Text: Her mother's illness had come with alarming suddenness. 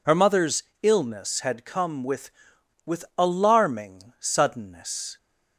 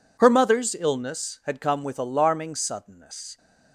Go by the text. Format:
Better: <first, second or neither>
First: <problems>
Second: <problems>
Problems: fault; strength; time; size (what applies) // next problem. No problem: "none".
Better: second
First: pauses between "mother's" and "illness"; slight; at 0.6 s; 0.18 s long // says "with" twice; at 2.8 s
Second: none